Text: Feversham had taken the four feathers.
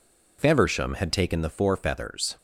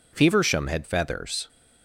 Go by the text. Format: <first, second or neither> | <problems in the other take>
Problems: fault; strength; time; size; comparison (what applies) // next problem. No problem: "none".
first | skips "taken the four"; at 0.8 s